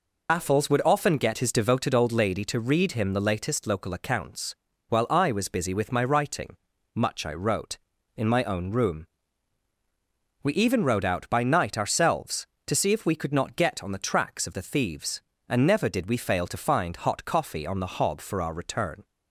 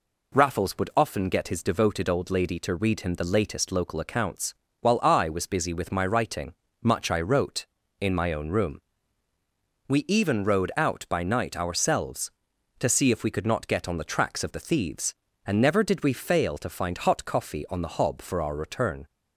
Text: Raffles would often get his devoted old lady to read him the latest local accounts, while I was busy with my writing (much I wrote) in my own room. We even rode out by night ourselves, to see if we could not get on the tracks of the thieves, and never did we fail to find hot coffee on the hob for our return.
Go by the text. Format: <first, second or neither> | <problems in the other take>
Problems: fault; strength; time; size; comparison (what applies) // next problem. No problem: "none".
second | loses the start of "Raffles"; at 0.2 s; 120 ms